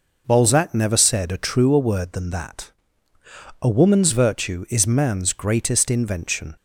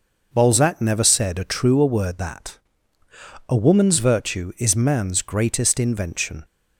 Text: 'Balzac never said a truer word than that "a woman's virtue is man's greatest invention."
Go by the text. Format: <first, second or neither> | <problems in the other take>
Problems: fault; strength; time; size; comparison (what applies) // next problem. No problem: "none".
first | skips "than"; at 2.1 s // pauses between "that" and "a"; noticeable; at 2.5 s; 0.90 s long; noticeable in the first